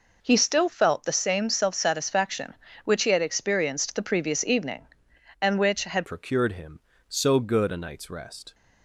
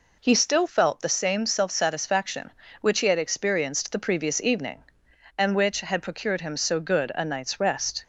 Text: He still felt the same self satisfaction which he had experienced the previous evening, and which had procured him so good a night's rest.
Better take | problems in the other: second | changes voice at "procured"; from 6.0 s on; 2.5 s long

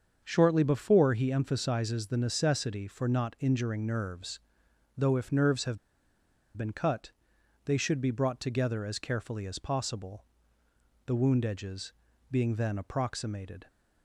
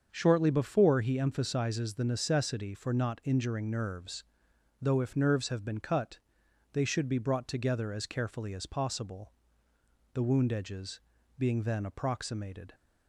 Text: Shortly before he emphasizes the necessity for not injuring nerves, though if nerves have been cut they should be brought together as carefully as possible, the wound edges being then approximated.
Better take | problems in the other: second | starts louder than the rest; until 1.2 s; 7 dB; also in the second // pauses between "have" and "been"; noticeable; at 5.7 s; 0.79 s long // pauses between "cut" and "they"; noticeable; at 7.1 s; 0.54 s long; noticeable in the second // pauses between "edges" and "being"; at 11.9 s; 0.40 s long; also in the second

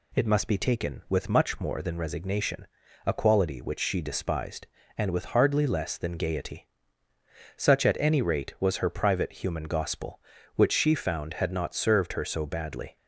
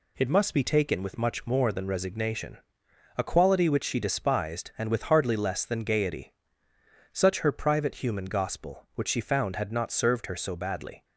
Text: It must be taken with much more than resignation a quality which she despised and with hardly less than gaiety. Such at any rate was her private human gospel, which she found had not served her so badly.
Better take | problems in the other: first | pauses between "resignation" and "a"; noticeable; at 2.5 s; 0.58 s long; also in the first // skips "at any rate was"; at 7.4 s

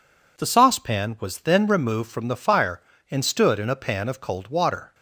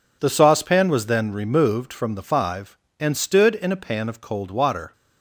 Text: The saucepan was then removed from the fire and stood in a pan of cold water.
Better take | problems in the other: first | says "five" for "fire"; at 2.2 s

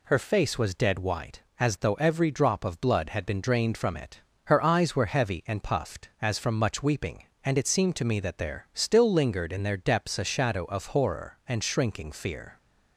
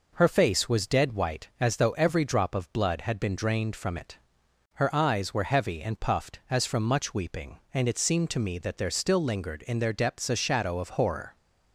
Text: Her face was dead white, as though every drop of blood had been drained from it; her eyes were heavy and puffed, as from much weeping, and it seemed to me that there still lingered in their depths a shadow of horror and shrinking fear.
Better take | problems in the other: first | stops before "and shrinking fear"; at 11.3 s

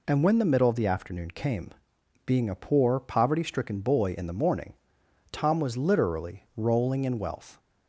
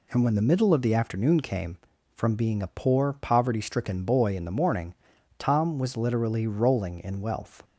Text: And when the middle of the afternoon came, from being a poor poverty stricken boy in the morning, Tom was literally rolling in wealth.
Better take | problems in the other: second | skips "from"; at 1.9 s

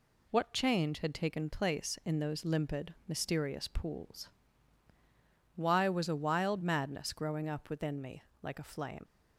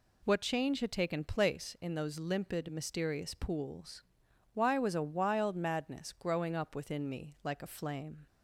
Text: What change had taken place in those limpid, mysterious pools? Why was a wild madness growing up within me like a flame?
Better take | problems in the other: second | pauses between "me" and "like"; slight; at 8.2 s; 0.20 s long // leaves "flame" unfinished; at 9.0 s; 90 ms

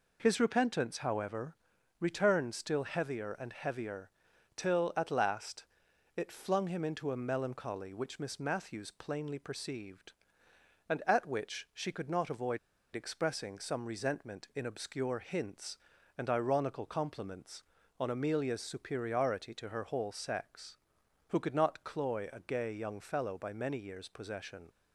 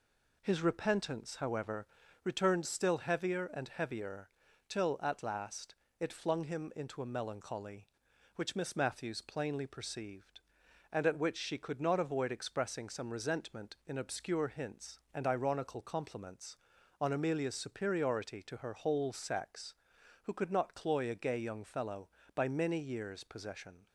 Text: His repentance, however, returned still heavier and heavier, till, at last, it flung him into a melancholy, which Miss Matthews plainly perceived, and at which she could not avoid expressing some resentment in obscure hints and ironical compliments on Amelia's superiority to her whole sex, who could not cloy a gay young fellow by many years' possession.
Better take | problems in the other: second | pauses between "avoid" and "expressing"; at 12.5 s; 0.36 s long

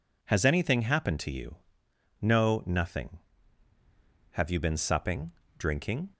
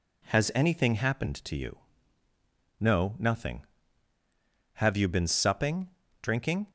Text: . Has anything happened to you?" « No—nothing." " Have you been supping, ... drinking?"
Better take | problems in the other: neither | none

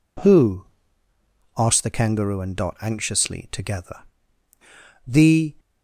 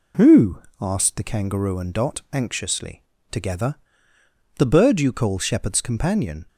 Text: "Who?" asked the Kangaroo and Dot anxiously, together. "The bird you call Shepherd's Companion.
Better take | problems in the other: second | stops before "bird you call Shepherd's Companion"; at 5.5 s

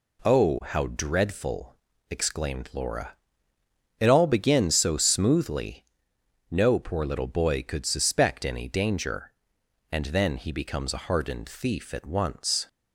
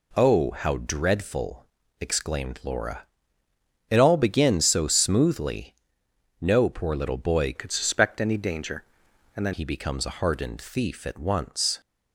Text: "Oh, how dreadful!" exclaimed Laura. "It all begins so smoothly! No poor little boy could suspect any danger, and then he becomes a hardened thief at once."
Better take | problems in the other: first | changes voice from "could" to "then"; from 7.5 to 9.5 s; 2.0 s long

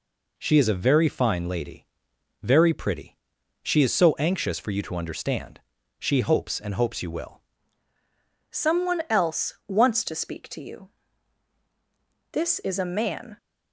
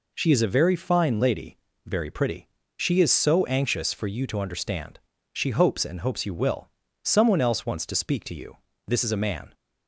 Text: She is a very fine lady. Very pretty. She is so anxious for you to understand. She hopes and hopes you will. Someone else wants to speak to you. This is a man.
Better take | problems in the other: second | changes voice at "Someone"; from 8.5 s on; 4.8 s long

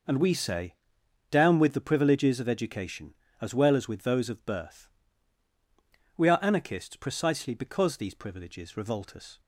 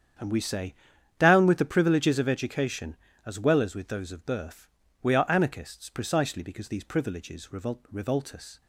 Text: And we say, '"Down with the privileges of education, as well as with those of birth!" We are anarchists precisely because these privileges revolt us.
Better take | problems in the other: first | starts louder than the rest; strong; until 1.6 s; 8.5 dB // says "revolt" twice; at 7.9 s

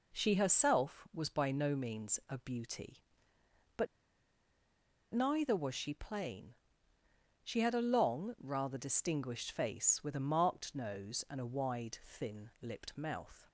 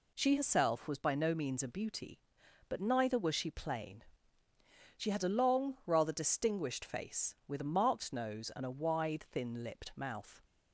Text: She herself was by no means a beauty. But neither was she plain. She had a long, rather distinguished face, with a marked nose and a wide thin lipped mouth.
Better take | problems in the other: second | pauses between "But" and "neither"; strong; at 3.8 s; 1.2 s long

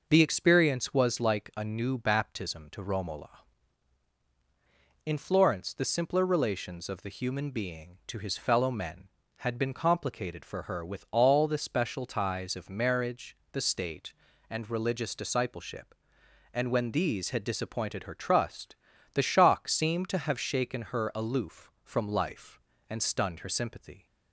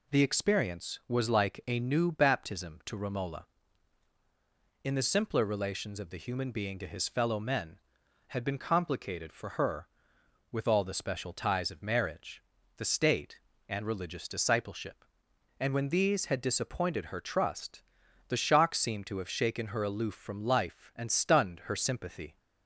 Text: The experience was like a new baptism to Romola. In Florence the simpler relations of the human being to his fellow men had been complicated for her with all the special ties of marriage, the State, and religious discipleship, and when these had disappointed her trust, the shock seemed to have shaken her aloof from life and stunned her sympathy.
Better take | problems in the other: first | skips "Florence"; at 4.9 s

